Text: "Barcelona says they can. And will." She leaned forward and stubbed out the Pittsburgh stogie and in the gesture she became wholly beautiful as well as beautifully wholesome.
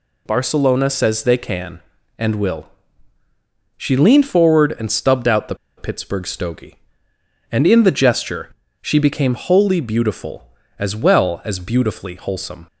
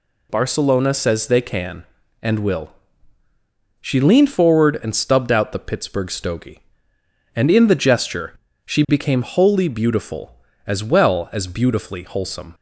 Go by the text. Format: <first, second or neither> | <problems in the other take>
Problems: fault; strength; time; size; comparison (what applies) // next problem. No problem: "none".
second | pauses between "the" and "Pittsburgh"; slight; at 5.5 s; 0.22 s long // pauses between "gesture" and "she"; slight; at 8.5 s; 0.30 s long; slight in the second